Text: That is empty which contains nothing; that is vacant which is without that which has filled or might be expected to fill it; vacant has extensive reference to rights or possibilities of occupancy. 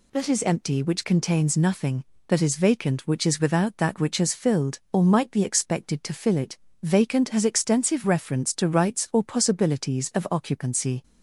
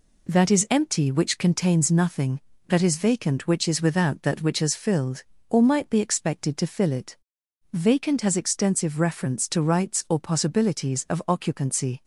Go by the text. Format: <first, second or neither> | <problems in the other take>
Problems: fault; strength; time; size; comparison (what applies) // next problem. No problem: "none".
neither | none